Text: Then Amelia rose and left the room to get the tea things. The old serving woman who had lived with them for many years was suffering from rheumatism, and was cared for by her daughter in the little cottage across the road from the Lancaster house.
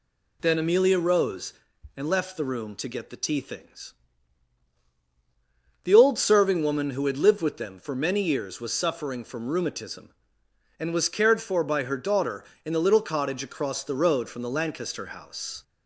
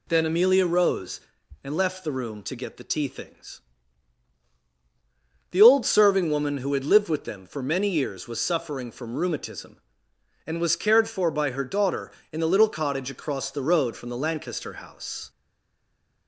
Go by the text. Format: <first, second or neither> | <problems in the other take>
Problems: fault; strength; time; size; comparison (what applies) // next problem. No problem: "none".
first | stays silent after the last word; from 15.2 s on; 1.0 s long